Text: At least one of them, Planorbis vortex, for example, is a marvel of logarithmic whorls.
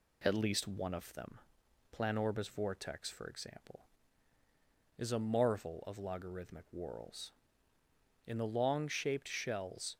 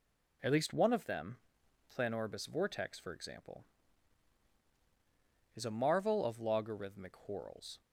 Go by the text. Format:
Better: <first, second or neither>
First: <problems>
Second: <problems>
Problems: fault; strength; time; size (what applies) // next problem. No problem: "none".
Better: second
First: goes on to say "In the long shaped shells"; strong; from 8.2 s on; 1.7 s long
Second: none